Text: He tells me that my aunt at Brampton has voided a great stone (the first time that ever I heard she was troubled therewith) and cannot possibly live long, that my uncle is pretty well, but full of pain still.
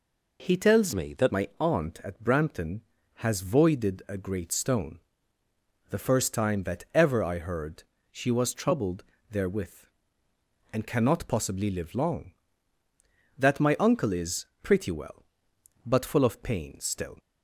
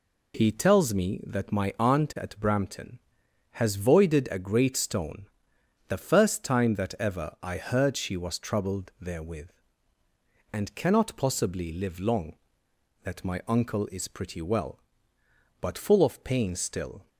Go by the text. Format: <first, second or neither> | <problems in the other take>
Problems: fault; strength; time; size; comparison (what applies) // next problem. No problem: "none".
second | changes voice from "me" to "that"; from 0.9 to 1.3 s; 0.4 s long // pauses between "heard" and "she"; slight; at 7.8 s; 0.28 s long // pauses between "troubled" and "therewith"; slight; at 9.0 s; 0.24 s long // pauses between "is" and "pretty"; slight; at 14.4 s; 0.16 s long